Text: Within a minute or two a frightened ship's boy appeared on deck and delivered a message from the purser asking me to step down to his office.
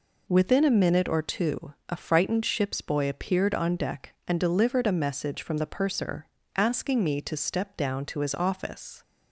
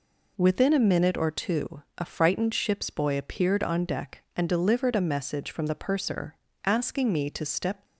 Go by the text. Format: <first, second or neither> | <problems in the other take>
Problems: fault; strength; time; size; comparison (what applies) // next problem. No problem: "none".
first | pauses between "two" and "a"; slight; at 1.8 s; 0.16 s long; slight in the first // pauses between "purser" and "asking"; slight; at 6.3 s; 0.30 s long; slight in the first // stops before "down to his office"; at 7.8 s